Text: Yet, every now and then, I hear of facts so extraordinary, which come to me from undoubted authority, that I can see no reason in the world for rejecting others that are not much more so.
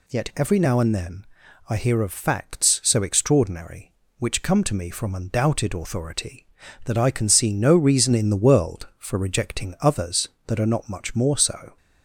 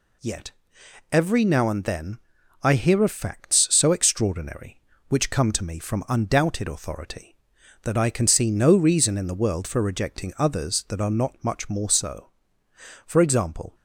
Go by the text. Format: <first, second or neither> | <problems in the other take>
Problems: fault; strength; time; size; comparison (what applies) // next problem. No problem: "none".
first | goes on to say "For example"; noticeable; from 13.0 s on; 0.68 s long